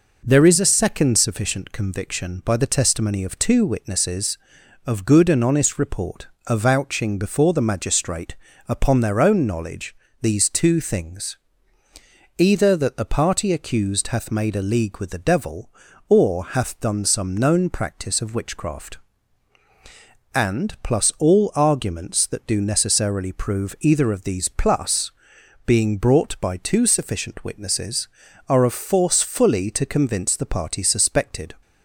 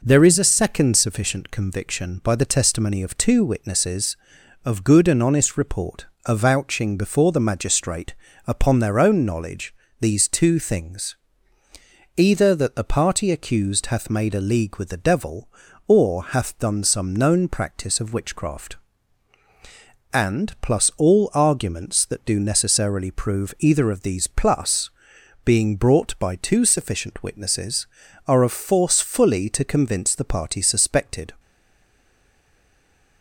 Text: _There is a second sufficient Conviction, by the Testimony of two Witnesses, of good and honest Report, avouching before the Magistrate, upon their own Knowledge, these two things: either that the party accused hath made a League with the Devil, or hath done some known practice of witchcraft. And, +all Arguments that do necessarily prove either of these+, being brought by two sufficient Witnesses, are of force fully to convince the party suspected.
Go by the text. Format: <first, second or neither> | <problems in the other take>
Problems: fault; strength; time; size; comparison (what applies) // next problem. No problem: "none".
first | stays silent after the last word; noticeable; from 31.3 s on; 1.9 s long